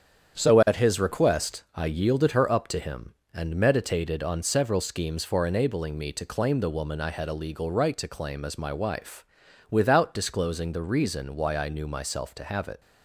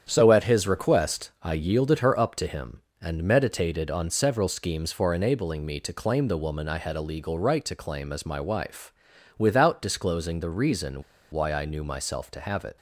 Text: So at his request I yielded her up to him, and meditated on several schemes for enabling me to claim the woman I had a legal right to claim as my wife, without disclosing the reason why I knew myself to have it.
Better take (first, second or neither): first